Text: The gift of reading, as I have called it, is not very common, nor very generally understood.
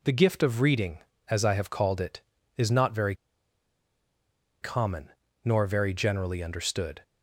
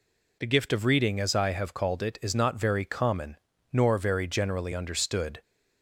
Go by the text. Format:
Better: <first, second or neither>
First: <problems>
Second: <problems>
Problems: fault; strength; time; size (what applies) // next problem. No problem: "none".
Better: second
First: pauses between "very" and "common"; strong; at 3.1 s; 1.4 s long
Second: none